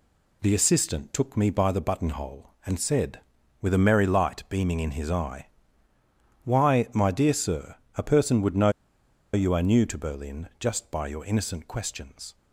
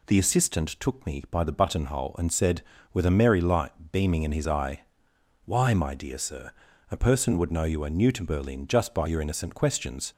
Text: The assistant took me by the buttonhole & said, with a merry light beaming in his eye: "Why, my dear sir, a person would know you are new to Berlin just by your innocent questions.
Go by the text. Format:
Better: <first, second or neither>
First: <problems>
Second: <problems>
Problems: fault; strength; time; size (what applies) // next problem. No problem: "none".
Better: second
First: pauses between "know" and "you"; noticeable; at 8.6 s; 0.64 s long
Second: none